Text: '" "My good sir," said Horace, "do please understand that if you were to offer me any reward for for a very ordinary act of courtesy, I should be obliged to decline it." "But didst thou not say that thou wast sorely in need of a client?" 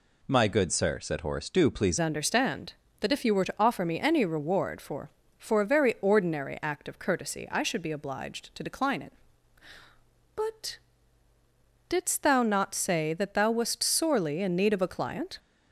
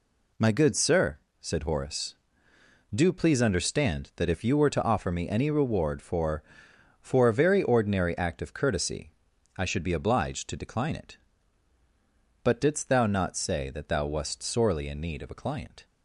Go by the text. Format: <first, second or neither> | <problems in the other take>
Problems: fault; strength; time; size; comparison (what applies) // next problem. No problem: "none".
second | changes voice at "understand"; from 1.9 s on; 13.4 s long // pauses between "But" and "didst"; at 10.7 s; 1.1 s long